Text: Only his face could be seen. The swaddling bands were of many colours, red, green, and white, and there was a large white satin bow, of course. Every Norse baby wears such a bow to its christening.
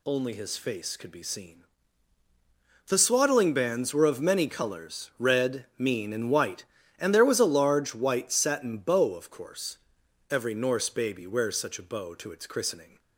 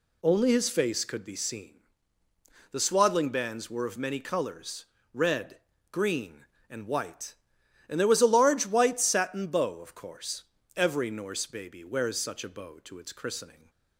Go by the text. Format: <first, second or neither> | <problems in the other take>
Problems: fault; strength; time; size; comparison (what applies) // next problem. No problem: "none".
second | says "mean" for "green"; at 5.7 s